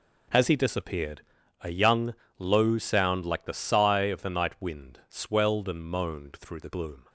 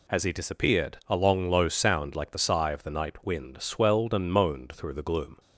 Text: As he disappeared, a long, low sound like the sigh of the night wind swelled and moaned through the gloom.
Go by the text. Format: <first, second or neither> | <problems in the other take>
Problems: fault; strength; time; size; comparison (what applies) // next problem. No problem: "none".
second | says "young" for "long"; at 1.6 s